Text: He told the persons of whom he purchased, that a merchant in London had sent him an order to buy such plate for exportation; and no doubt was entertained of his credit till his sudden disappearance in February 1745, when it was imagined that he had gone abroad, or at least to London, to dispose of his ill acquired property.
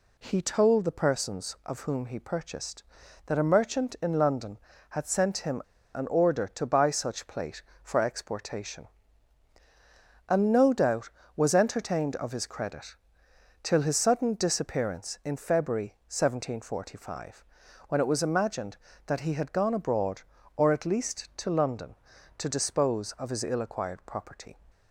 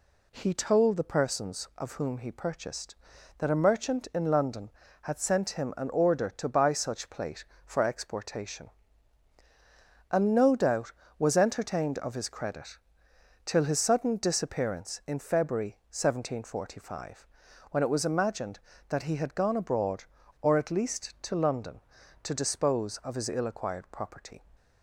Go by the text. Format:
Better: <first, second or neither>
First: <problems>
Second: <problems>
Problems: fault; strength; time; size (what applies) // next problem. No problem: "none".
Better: second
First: pauses between "him" and "an"; slight; at 5.6 s; 0.33 s long // pauses between "credit" and "till"; noticeable; at 12.9 s; 0.68 s long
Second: pauses between "credit" and "till"; noticeable; at 12.7 s; 0.68 s long